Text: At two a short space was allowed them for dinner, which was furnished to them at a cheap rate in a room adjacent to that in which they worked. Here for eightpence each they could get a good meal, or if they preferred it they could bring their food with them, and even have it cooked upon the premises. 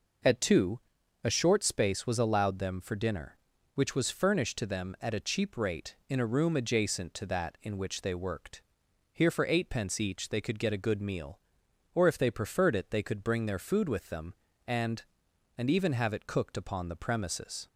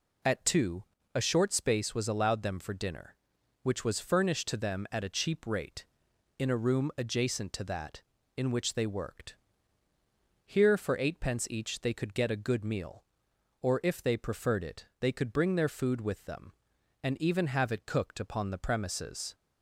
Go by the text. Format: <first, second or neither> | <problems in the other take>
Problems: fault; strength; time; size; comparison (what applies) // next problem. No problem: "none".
second | pauses between "two" and "a"; noticeable; at 0.7 s; 0.46 s long; slight in the second // says "and" twice; at 15.5 s